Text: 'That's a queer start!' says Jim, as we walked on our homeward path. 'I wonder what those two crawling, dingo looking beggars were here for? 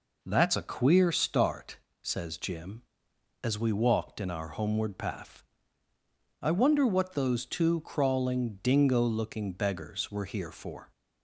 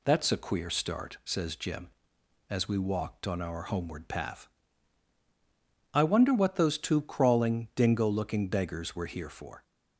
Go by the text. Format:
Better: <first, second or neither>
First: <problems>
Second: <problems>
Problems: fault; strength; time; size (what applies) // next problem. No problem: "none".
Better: second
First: says "in" for "on"; at 4.1 s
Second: none